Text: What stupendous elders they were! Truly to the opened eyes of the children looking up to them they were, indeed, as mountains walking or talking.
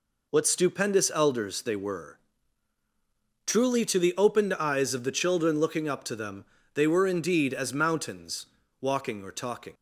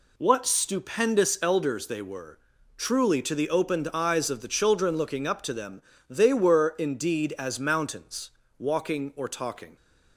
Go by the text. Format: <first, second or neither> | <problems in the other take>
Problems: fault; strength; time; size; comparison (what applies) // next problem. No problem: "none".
neither | pauses between "them" and "they"; slight; the same in both // pauses between "mountains" and "walking"; slight; the same in both